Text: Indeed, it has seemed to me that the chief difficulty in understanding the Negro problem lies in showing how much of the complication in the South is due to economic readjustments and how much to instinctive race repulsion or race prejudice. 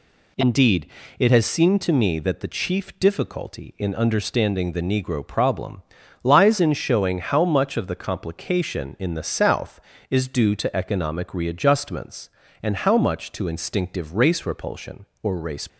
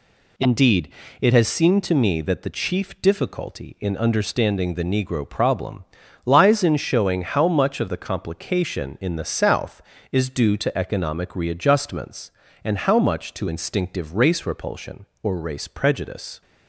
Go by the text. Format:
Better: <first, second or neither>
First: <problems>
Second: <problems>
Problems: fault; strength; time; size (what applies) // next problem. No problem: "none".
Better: second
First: pauses between "problem" and "lies"; at 5.8 s; 0.42 s long // stops before "prejudice"; at 15.6 s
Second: pauses between "problem" and "lies"; at 5.8 s; 0.42 s long